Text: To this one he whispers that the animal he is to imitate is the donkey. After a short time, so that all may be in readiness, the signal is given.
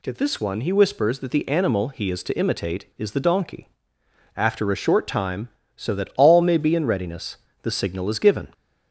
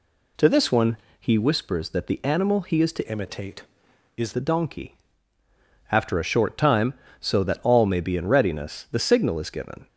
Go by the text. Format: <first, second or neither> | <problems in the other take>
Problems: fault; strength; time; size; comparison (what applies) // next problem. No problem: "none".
first | pauses between "one" and "he"; slight; at 0.9 s; 0.22 s long // changes voice from "imitate" to "is"; from 3.0 to 4.3 s; 1.3 s long